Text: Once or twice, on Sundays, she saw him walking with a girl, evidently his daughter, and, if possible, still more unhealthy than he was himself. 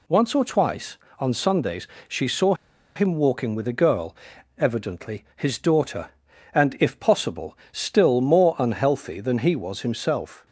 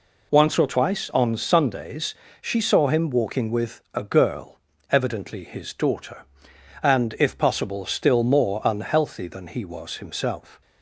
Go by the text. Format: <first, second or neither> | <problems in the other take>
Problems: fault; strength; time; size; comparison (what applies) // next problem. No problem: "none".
second | pauses between "saw" and "him"; at 2.5 s; 0.41 s long